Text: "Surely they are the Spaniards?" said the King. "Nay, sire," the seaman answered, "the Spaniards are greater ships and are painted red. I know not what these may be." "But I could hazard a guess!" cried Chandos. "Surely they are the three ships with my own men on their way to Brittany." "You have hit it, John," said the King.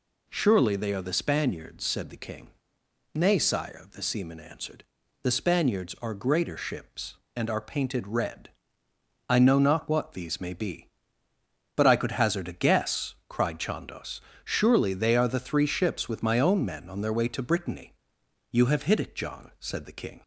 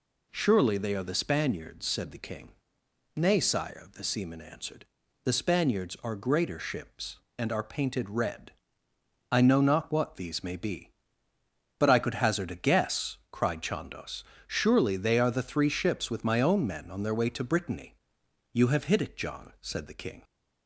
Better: neither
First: none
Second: none

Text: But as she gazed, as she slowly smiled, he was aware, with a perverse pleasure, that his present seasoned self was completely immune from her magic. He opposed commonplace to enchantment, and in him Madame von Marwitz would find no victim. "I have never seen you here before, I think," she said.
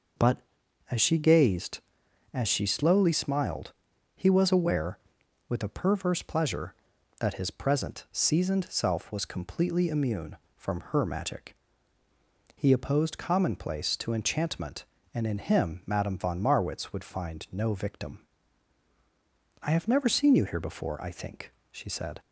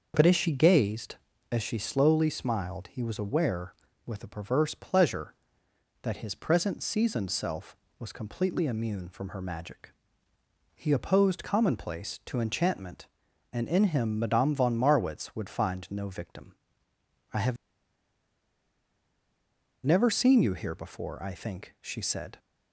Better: first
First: none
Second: starts louder than the rest; until 1.1 s; 6.5 dB // pauses between "have" and "never"; strong; at 17.5 s; 2.3 s long

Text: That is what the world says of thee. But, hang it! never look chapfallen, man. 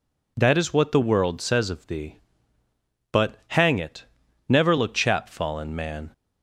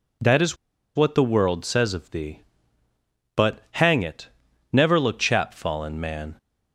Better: first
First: none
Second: pauses between "is" and "what"; at 0.5 s; 0.39 s long

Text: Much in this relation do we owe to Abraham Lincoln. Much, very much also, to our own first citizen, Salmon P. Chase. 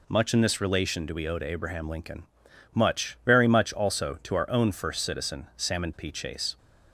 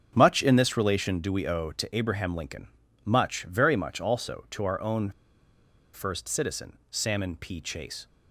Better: first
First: none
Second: starts louder than the rest; strong; until 1.1 s; 7 dB // pauses between "own" and "first"; noticeable; at 5.0 s; 0.83 s long

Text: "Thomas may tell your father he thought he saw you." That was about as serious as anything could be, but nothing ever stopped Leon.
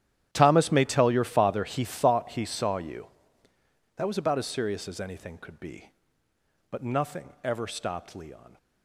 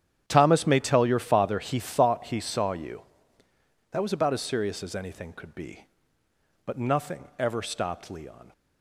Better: second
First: gets quieter; strong; throughout; 18 dB // starts louder than the rest; strong; until 1.3 s; 11 dB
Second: starts louder than the rest; strong; until 1.2 s; 9.5 dB

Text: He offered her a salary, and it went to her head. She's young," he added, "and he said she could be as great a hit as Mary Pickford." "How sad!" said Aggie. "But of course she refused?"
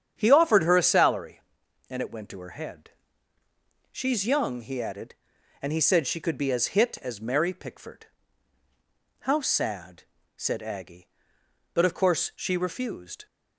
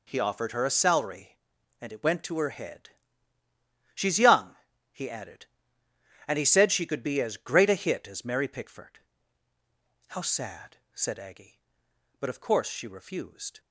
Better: second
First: starts louder than the rest; strong; until 1.1 s; 8.5 dB // skips "great a"; at 6.7 s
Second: none

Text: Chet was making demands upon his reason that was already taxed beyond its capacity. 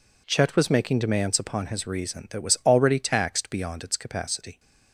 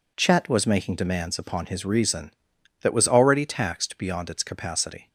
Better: neither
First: none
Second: none

